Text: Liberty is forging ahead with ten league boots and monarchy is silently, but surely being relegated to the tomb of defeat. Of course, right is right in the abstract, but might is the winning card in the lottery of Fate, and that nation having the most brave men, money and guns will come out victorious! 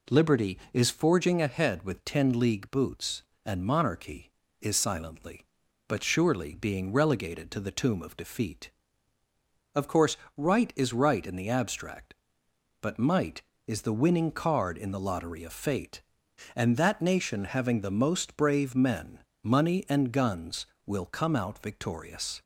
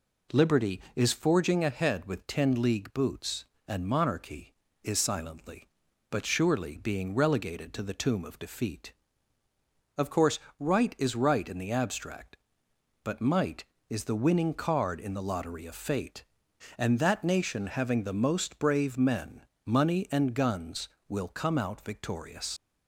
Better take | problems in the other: first | leaves "victorious" unfinished; at 22.5 s; 75 ms

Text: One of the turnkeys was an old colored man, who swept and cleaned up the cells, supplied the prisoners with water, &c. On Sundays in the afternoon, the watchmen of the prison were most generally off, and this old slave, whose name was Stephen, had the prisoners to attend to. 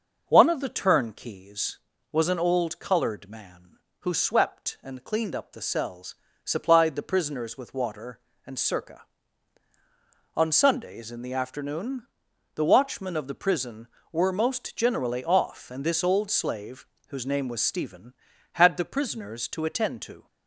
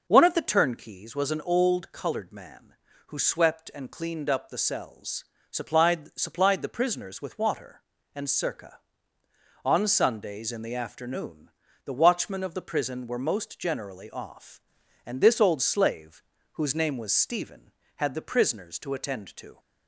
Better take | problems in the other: first | says "supplied" twice; at 6.1 s

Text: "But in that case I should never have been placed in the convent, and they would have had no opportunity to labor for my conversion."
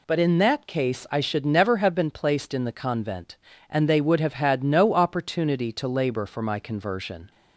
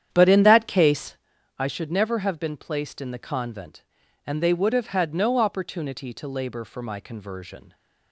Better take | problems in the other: first | starts louder than the rest; strong; until 1.2 s; 9.5 dB // pauses between "case" and "I"; at 1.1 s; 0.40 s long

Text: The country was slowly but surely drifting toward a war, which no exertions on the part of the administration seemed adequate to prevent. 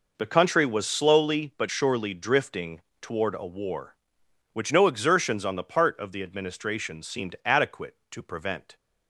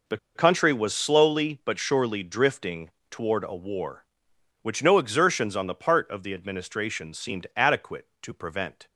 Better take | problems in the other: first | pauses between "The" and "country"; slight; at 0.1 s; 0.19 s long // pauses between "drifting" and "toward"; slight; at 2.9 s; 0.20 s long; slight in the first

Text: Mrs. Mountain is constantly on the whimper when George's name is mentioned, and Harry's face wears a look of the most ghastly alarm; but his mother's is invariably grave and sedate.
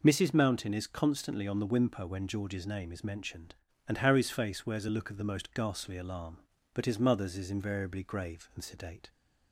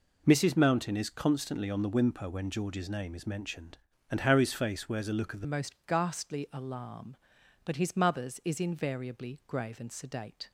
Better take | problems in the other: first | changes voice at "most"; from 5.4 s on; 5.1 s long

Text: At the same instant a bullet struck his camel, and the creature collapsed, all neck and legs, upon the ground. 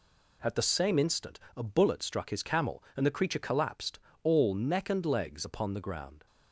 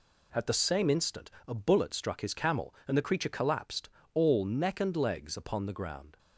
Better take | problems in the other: neither | pauses between "instant" and "a"; slight; the same in both

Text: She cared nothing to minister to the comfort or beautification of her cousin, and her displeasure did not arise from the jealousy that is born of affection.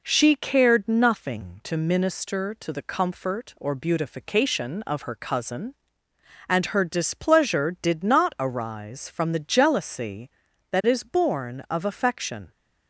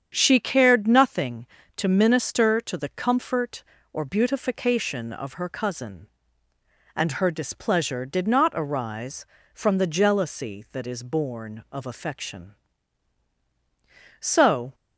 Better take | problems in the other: first | starts louder than the rest; strong; until 1.1 s; 8 dB // goes on to say "So"; from 14.2 s on; 0.54 s long

